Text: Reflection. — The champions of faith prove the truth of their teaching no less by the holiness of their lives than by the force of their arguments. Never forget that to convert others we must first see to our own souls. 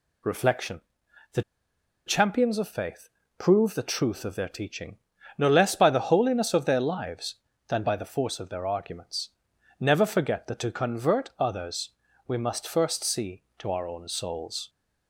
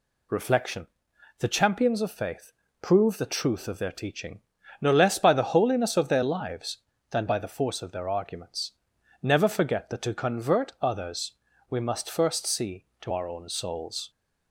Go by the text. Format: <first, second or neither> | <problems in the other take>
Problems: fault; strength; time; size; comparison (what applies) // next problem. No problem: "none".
second | pauses between "The" and "champions"; noticeable; at 1.4 s; 0.63 s long // pauses between "faith" and "prove"; slight; at 3.0 s; 0.30 s long; slight in the second // pauses between "teaching" and "no"; at 4.9 s; 0.40 s long; also in the second // pauses between "others" and "we"; slight; at 11.8 s; 0.36 s long; slight in the second